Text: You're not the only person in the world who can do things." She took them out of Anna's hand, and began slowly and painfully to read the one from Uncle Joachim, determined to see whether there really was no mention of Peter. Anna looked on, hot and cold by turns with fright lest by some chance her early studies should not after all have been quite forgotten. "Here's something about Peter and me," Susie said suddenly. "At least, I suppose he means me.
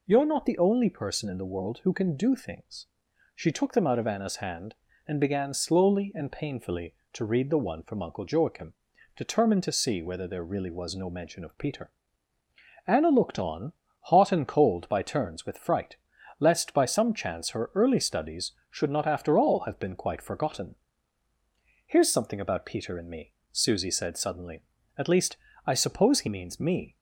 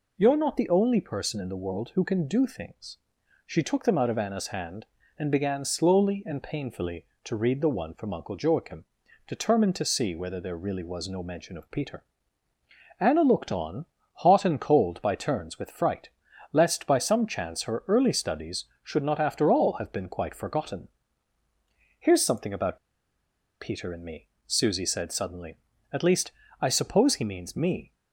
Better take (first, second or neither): first